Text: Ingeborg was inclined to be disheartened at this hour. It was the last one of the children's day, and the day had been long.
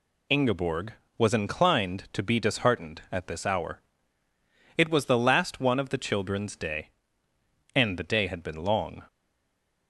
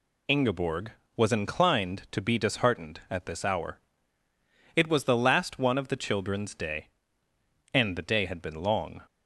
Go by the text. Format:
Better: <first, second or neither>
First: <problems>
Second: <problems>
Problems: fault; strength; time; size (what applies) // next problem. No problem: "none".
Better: second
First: stays silent after the last word; slight; from 9.0 s on; 0.8 s long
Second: none